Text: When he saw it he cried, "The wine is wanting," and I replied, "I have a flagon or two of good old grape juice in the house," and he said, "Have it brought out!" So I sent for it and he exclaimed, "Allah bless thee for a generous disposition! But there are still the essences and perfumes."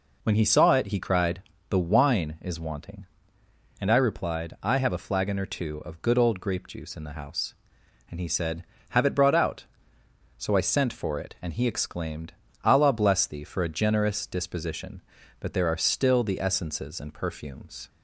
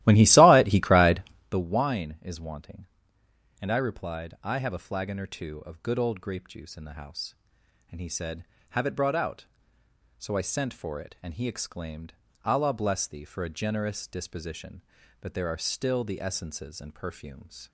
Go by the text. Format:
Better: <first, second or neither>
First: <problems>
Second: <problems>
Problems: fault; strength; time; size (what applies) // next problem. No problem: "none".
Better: first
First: none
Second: starts louder than the rest; strong; until 1.6 s; 15.5 dB